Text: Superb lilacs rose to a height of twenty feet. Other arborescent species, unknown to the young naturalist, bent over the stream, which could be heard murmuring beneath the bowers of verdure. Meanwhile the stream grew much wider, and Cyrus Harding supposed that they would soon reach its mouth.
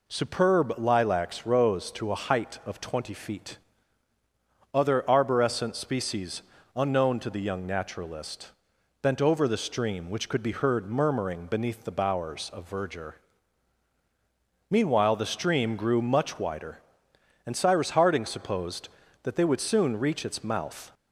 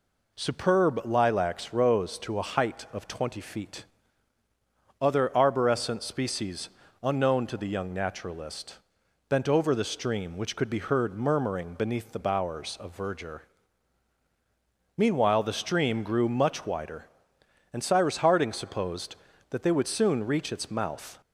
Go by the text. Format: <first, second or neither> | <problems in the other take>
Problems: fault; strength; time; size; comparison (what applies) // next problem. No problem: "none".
neither | none